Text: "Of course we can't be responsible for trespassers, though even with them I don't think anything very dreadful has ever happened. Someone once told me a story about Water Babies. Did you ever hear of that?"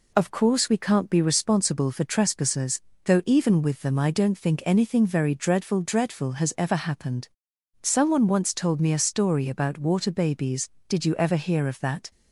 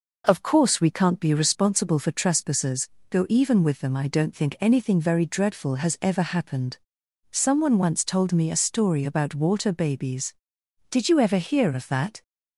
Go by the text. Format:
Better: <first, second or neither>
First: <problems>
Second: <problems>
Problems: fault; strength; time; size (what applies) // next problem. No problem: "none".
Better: second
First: says "dreadful" twice; at 5.8 s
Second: none